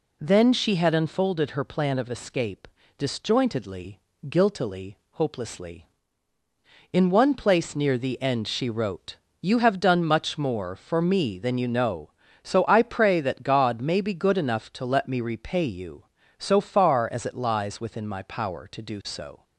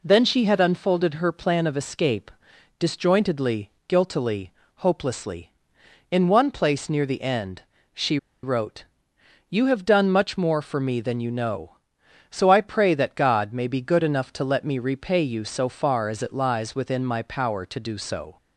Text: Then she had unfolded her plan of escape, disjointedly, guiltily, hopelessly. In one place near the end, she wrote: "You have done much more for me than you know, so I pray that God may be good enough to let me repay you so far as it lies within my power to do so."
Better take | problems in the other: first | pauses between "she" and "wrote"; slight; at 8.1 s; 0.26 s long

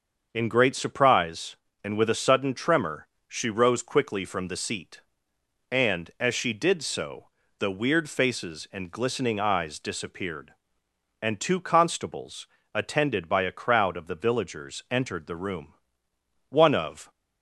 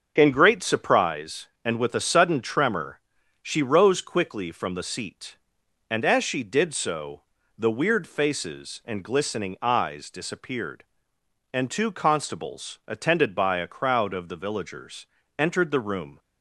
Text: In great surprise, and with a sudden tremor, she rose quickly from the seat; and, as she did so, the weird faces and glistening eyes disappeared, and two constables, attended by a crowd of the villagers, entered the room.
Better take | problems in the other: second | starts louder than the rest; until 1.3 s; 6.5 dB; also in the second // goes on to say "One of"; noticeable; from 16.4 s on; 0.62 s long

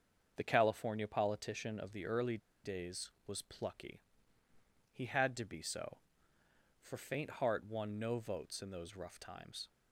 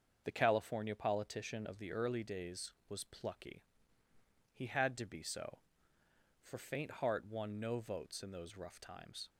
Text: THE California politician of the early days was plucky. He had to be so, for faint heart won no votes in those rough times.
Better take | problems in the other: second | starts louder than the rest; until 1.3 s; 7 dB; also in the second // pauses between "early" and "days"; slight; at 2.3 s; 0.26 s long

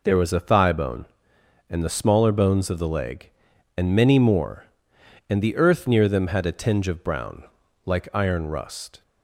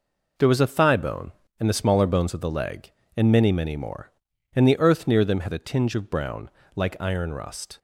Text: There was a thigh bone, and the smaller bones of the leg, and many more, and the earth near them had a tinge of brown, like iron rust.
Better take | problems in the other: first | says "many" twice; at 3.5 s

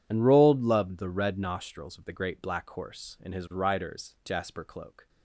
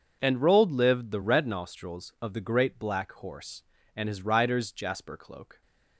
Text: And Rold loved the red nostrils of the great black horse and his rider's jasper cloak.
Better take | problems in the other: first | says "lived" for "loved"; at 0.7 s

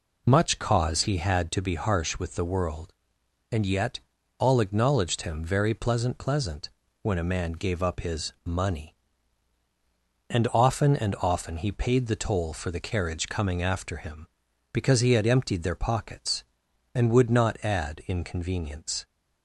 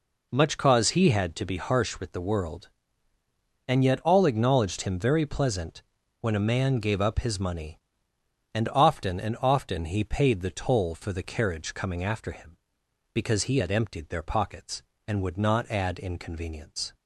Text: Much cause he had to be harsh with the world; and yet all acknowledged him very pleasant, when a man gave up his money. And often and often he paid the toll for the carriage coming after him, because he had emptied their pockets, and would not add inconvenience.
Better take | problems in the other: second | pauses between "yet" and "all"; at 3.9 s; 0.40 s long // says "pleasant" twice; at 6.1 s

